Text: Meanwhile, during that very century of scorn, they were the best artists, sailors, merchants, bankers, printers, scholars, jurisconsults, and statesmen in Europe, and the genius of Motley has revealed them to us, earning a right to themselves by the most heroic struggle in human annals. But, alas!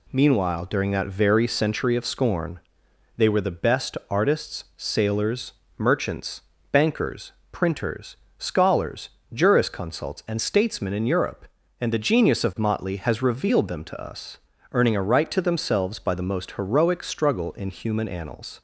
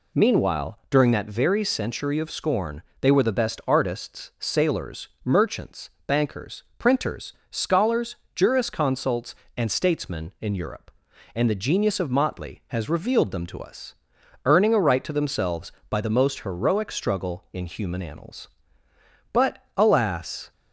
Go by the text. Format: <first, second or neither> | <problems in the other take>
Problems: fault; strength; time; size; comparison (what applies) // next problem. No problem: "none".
second | stops before "But alas"; at 18.5 s